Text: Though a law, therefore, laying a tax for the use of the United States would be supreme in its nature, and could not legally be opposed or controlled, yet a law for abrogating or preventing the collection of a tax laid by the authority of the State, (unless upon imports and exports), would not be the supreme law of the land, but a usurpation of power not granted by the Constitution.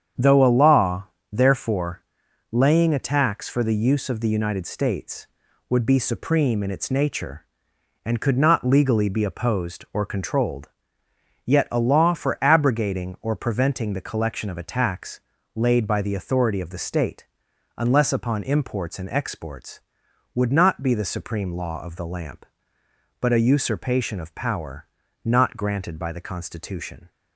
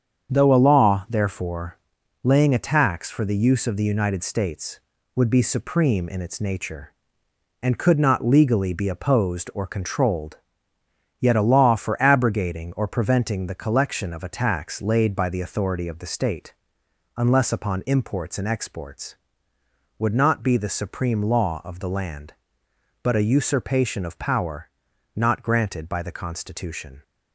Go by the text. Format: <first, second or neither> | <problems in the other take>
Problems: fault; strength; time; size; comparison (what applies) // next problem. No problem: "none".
second | starts louder than the rest; strong; until 1.4 s; 8 dB; strong in the second // pauses between "tax" and "laid"; slight; at 15.2 s; 0.34 s long // says "lamp" for "land"; at 22.0 s // pauses between "power" and "not"; slight; at 24.8 s; 0.36 s long; also in the second